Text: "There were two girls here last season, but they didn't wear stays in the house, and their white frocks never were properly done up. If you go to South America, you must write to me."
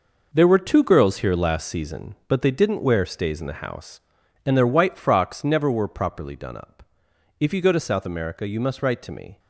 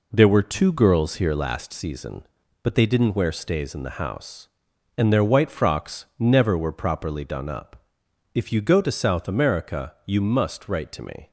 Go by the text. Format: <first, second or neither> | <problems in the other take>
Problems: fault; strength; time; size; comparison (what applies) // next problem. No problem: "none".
second | gets quieter; strong; throughout; 9.5 dB